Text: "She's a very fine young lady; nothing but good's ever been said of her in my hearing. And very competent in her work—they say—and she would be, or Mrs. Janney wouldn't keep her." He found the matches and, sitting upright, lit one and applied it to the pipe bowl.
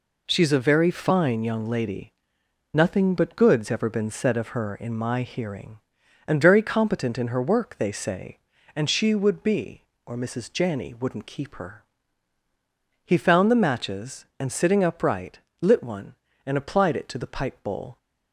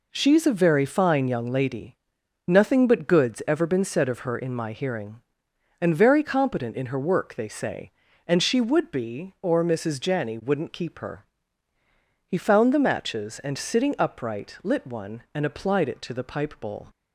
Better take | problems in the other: neither | none

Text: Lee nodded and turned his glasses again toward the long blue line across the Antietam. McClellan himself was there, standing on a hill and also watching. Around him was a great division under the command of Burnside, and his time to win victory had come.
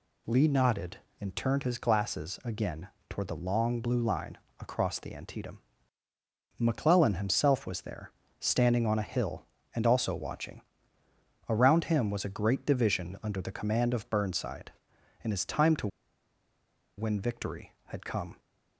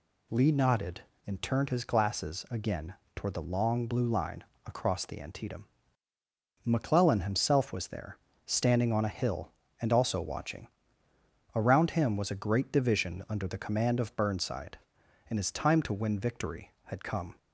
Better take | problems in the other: second | pauses between "again" and "toward"; slight; at 2.8 s; 0.22 s long; slight in the second // pauses between "line" and "across"; slight; at 4.3 s; 0.22 s long; slight in the second // pauses between "to" and "win"; at 15.8 s; 1.1 s long

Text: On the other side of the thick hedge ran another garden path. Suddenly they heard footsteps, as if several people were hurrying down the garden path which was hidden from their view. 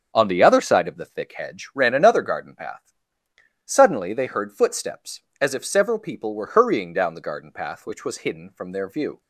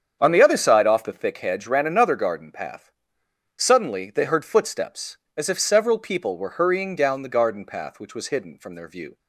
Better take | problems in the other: first | starts louder than the rest; strong; until 1.2 s; 8 dB; strong in the first // says "off" for "of"; at 0.8 s

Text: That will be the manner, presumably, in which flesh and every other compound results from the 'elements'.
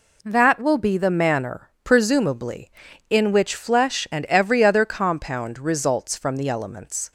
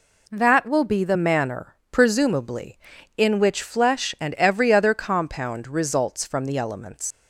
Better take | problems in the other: first | leaves "elements" unfinished; at 7.1 s; 95 ms

